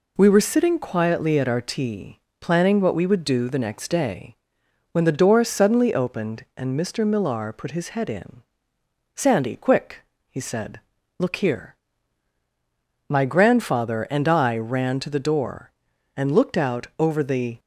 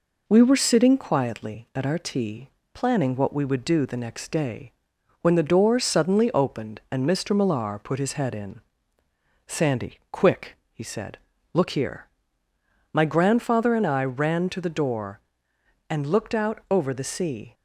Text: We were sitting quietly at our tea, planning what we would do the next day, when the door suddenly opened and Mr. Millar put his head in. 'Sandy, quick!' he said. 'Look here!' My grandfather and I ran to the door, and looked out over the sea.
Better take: second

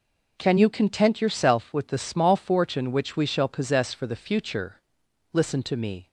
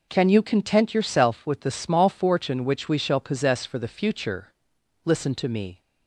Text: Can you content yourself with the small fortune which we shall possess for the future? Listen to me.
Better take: neither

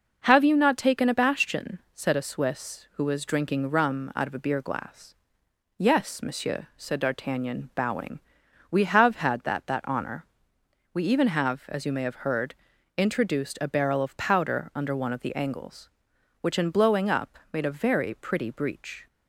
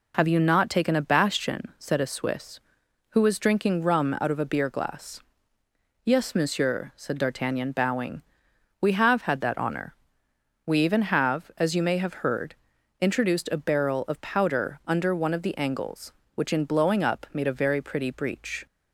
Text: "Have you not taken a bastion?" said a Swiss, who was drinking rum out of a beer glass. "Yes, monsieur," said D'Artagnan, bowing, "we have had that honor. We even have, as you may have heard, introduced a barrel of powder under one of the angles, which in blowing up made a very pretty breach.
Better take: second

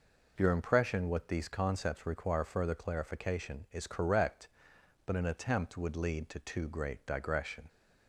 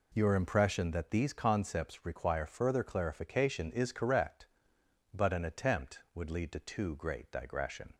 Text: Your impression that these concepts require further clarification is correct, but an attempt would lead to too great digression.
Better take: second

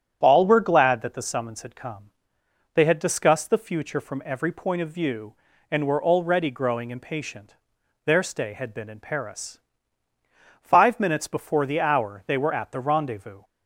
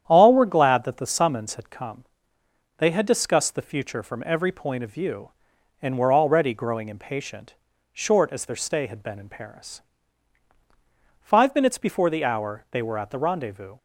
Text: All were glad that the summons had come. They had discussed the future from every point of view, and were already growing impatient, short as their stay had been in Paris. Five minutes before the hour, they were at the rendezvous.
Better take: second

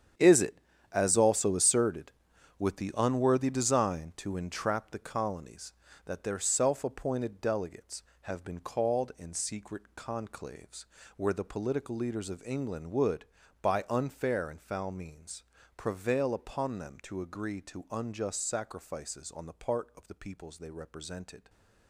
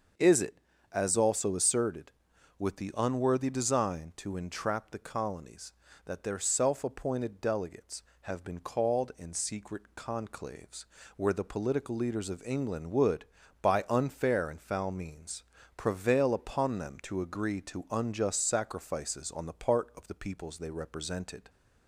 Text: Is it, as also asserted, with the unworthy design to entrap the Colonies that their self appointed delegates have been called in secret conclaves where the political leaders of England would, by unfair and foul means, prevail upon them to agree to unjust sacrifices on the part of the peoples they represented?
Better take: second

